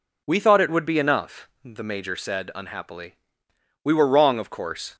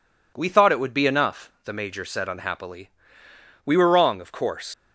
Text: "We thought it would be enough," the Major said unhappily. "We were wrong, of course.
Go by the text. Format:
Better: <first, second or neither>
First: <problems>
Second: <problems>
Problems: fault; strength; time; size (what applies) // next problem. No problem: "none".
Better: first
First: none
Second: leaves "course" unfinished; at 4.7 s; 70 ms